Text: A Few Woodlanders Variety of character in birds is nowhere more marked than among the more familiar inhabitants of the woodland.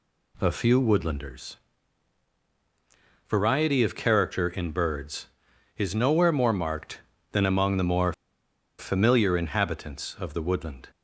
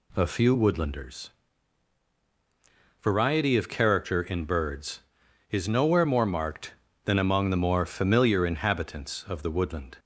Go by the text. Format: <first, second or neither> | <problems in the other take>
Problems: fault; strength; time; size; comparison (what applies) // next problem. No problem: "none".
second | pauses between "Woodlanders" and "Variety"; strong; at 1.5 s; 1.7 s long; strong in the second // pauses between "more" and "familiar"; noticeable; at 8.1 s; 0.66 s long